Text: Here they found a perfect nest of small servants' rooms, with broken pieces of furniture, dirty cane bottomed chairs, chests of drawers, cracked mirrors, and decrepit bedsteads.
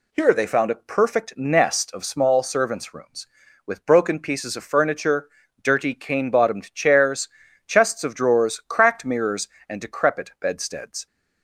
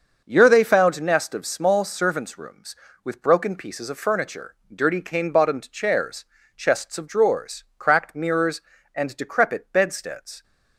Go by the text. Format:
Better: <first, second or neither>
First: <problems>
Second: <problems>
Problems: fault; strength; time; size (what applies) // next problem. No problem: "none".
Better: first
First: none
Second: starts louder than the rest; noticeable; until 1.2 s; 6 dB // skips "a perfect"; at 1.0 s